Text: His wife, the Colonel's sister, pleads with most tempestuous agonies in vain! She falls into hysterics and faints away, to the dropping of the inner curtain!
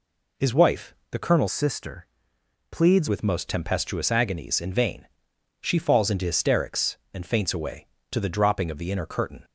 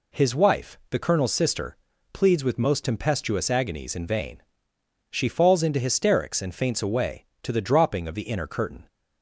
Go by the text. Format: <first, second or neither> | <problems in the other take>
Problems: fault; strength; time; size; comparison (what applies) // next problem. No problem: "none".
second | changes voice from "sister" to "pleads"; from 1.5 to 3.0 s; 1.5 s long